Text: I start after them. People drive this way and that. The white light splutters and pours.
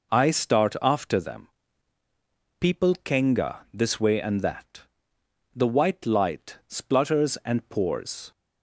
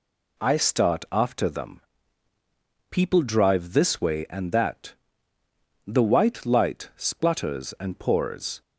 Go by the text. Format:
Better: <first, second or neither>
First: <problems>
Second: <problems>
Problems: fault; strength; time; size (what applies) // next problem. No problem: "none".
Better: second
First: says "kenga" for "drive"; at 3.0 s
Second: none